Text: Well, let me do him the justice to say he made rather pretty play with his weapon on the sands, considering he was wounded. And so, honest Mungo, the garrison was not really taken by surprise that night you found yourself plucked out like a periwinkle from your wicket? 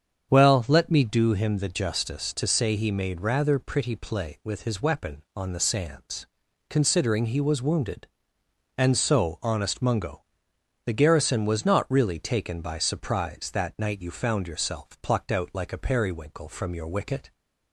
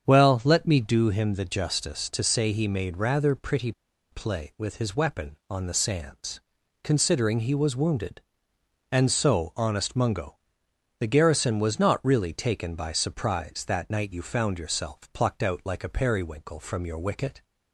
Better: first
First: starts louder than the rest; strong; until 1.3 s; 7.5 dB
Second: starts louder than the rest; strong; until 1.1 s; 7.5 dB // pauses between "pretty" and "play"; at 3.7 s; 0.40 s long

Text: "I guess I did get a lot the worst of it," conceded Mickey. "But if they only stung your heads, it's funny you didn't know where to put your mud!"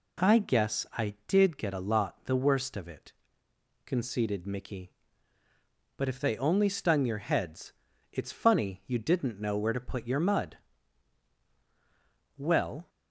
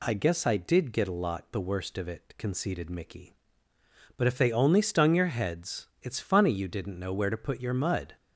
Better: second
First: goes on to say "Well"; from 12.3 s on; 0.52 s long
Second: none

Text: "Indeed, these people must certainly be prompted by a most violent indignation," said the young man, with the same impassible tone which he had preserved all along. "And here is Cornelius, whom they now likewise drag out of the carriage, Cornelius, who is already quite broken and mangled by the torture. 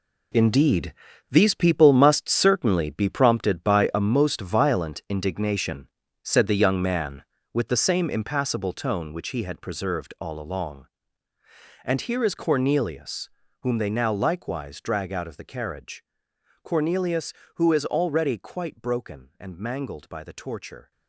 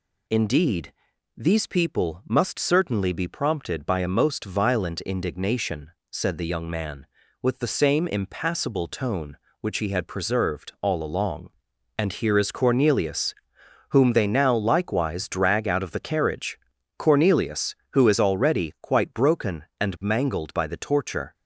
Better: second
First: gets quieter; strong; throughout; 11.5 dB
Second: none

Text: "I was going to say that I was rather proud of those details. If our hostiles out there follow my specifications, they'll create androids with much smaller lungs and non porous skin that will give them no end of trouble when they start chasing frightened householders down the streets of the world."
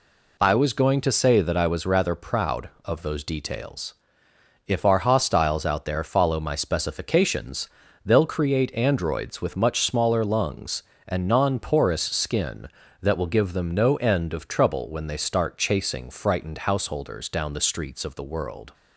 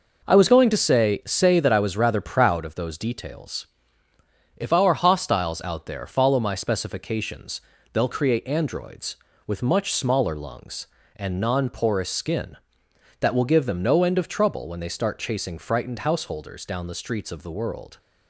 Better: first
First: none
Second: says "say" twice; at 1.2 s

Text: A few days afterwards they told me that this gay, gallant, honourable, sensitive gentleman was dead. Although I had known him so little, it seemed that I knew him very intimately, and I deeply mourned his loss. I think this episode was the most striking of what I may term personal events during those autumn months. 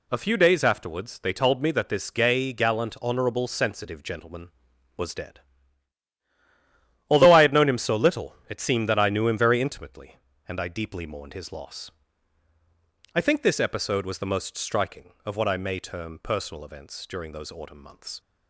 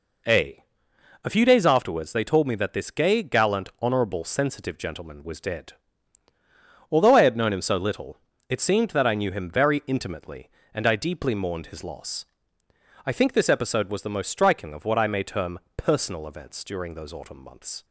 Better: first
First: none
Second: says "A" twice; at 1.2 s // pauses between "term" and "personal"; slight; at 15.5 s; 0.16 s long

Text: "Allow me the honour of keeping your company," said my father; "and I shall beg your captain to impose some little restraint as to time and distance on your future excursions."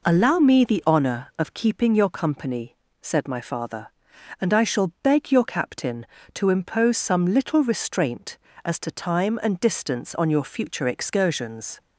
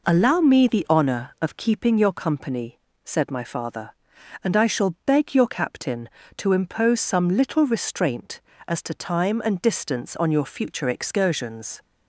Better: neither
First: none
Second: none

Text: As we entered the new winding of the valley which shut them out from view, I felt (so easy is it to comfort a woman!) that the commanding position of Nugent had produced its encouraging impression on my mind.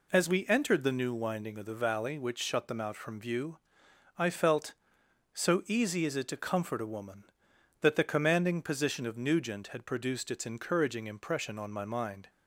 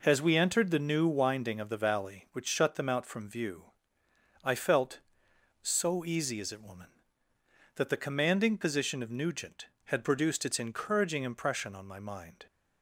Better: first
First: none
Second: skips "to comfort a"; at 6.6 s

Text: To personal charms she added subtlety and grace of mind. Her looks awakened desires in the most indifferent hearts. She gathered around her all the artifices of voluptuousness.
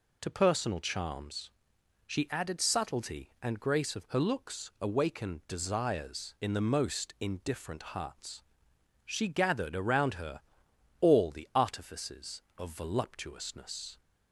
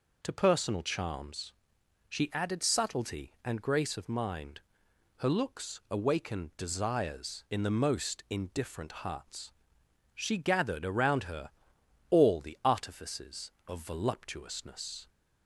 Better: second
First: pauses between "charms" and "she"; noticeable; at 1.5 s; 0.54 s long // skips "mind"; at 4.0 s // pauses between "her" and "all"; noticeable; at 10.4 s; 0.58 s long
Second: pauses between "charms" and "she"; noticeable; at 1.5 s; 0.54 s long // pauses between "her" and "all"; noticeable; at 11.5 s; 0.58 s long

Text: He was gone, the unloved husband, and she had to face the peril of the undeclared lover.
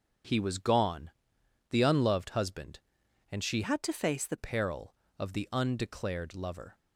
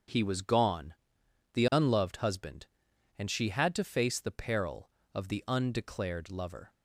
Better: second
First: starts louder than the rest; until 1.8 s; 7 dB // changes voice from "had" to "the"; from 3.6 to 4.3 s; 0.7 s long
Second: starts louder than the rest; until 1.6 s; 7 dB

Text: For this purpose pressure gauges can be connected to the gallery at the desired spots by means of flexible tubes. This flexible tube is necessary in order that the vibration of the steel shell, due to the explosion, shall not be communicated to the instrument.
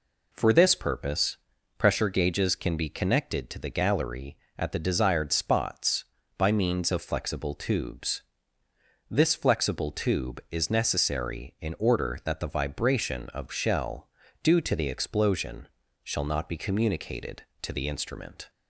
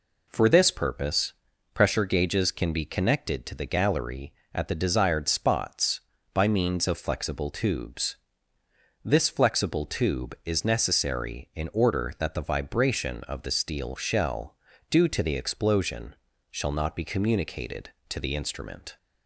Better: second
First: pauses between "purpose" and "pressure"; at 1.3 s; 0.42 s long // skips "the steel"; at 13.4 s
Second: pauses between "purpose" and "pressure"; at 1.3 s; 0.42 s long

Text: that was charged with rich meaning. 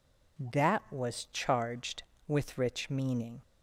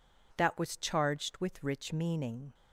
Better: neither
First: none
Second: none

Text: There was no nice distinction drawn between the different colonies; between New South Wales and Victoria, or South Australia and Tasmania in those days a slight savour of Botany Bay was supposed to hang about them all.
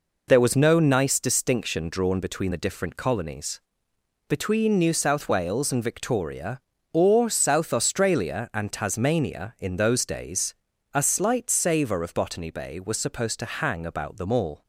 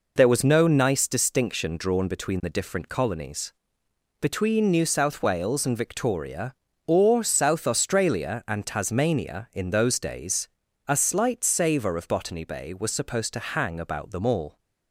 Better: neither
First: pauses between "days" and "a"; at 10.5 s; 0.40 s long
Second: pauses between "days" and "a"; at 10.4 s; 0.40 s long

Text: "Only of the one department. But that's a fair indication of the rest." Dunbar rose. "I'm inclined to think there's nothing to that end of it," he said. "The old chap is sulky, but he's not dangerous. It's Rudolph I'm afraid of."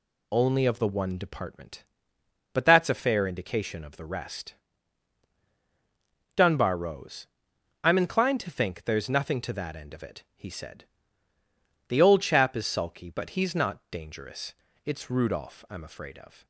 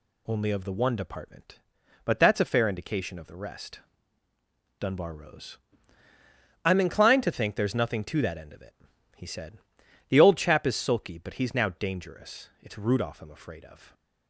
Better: first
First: none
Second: says "now" for "not"; at 11.5 s

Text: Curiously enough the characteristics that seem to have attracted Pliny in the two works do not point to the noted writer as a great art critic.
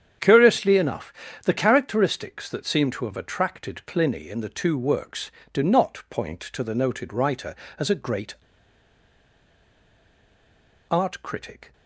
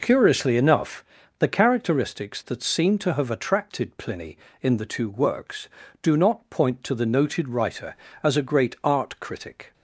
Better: second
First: starts louder than the rest; strong; until 1.5 s; 8.5 dB // pauses between "enough" and "the"; slight; at 1.1 s; 0.32 s long // pauses between "great" and "art"; strong; at 8.3 s; 2.5 s long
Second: pauses between "enough" and "the"; slight; at 1.0 s; 0.32 s long

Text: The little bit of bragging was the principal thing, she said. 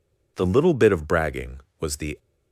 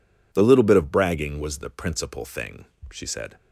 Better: second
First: stops before "principal thing she said"; at 2.1 s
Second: none

